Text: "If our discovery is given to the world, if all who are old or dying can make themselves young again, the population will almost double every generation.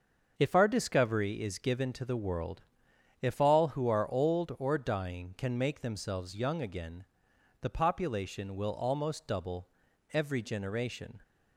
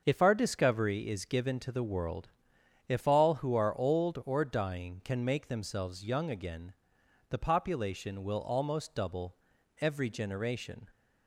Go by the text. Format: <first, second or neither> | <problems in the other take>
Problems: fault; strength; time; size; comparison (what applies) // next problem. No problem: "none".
neither | starts louder than the rest; the same in both // pauses between "double" and "every"; the same in both